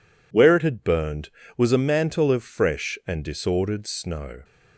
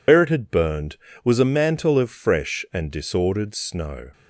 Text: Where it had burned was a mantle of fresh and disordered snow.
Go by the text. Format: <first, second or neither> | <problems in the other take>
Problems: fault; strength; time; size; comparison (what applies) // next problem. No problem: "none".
first | loses the start of "Where"; at 0.0 s; 105 ms